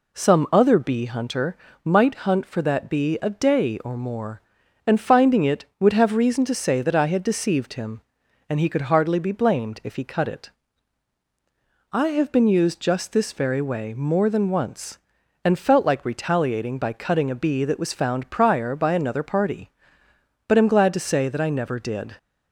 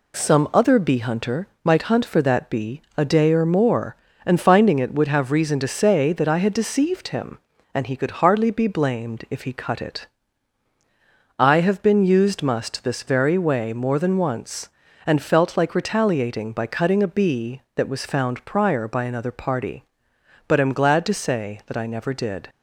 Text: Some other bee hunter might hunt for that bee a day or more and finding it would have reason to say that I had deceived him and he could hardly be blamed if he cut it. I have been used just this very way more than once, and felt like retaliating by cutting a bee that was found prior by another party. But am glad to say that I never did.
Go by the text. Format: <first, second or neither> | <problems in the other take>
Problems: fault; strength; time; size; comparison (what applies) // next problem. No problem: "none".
first | pauses between "hunter" and "might"; slight; at 1.4 s; 0.18 s long; slight in the first // says "must" for "just"; at 12.4 s